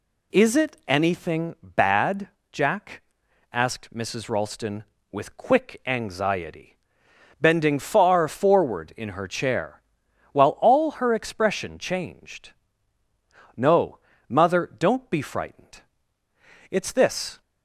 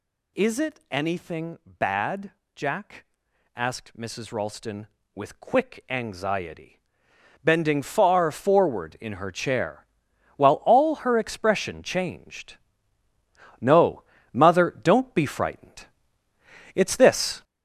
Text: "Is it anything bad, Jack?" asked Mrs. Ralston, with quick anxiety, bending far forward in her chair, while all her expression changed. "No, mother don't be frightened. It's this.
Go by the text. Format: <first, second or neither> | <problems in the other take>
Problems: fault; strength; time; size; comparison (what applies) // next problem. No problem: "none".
first | gets louder; strong; throughout; 7 dB